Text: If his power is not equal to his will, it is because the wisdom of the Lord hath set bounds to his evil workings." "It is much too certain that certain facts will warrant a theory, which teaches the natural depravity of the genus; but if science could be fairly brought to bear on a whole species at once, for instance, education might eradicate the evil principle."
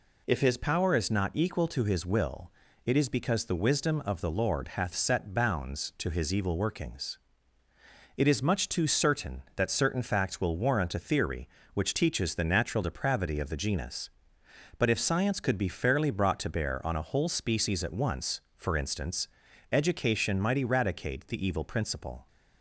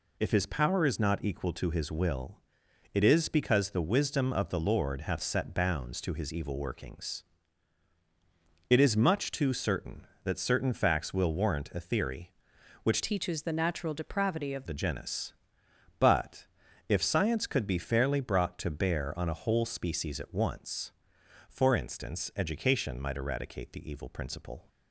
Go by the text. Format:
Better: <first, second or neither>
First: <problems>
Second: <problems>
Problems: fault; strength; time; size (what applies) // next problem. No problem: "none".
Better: first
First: none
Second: changes voice from "teaches" to "of"; from 13.0 to 14.6 s; 1.6 s long // pauses between "but" and "if"; at 16.4 s; 0.44 s long